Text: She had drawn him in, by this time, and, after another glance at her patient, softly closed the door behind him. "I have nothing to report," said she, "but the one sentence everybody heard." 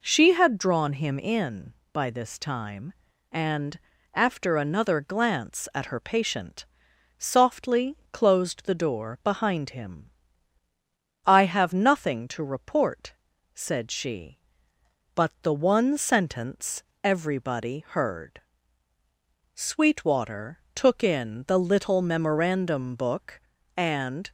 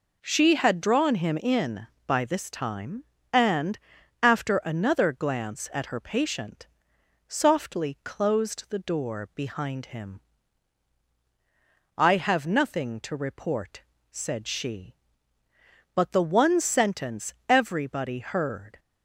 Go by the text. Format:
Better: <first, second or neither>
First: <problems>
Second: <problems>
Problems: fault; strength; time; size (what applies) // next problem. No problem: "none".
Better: second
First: pauses between "sentence" and "everybody"; slight; at 16.8 s; 0.22 s long // goes on to say "Sweetwater took in the little memorandum book and"; strong; from 19.5 s on; 4.7 s long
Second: pauses between "sentence" and "everybody"; slight; at 17.3 s; 0.16 s long